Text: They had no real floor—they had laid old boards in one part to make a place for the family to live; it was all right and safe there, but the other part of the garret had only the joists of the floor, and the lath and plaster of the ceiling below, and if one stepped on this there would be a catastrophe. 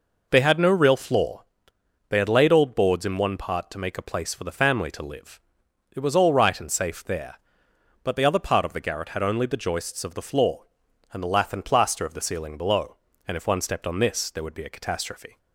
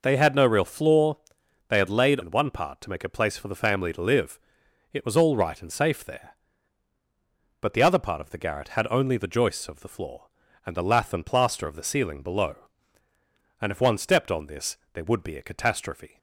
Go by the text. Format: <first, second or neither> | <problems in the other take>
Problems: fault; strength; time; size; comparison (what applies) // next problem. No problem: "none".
first | skips "old boards"; at 2.2 s // pauses between "this" and "there"; slight; at 14.7 s; 0.16 s long